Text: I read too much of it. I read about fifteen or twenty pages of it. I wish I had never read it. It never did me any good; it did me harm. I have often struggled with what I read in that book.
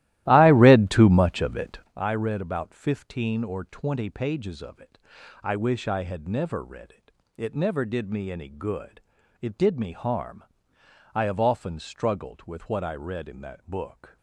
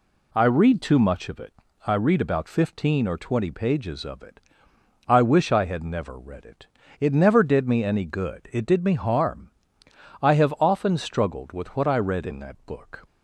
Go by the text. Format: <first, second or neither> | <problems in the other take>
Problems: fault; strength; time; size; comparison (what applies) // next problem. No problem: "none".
second | starts louder than the rest; strong; until 2.0 s; 16 dB